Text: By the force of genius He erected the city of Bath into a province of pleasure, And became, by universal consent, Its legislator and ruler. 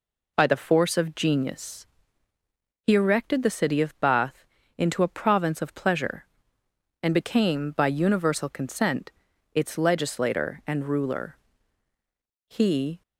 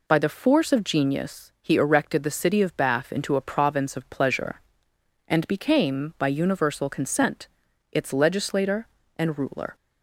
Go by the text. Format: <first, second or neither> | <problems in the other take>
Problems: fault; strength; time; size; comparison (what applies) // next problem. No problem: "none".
second | pauses between "genius" and "He"; at 1.8 s; 1.0 s long // pauses between "Bath" and "into"; slight; at 4.4 s; 0.32 s long // goes on to say "He"; from 12.4 s on; 0.54 s long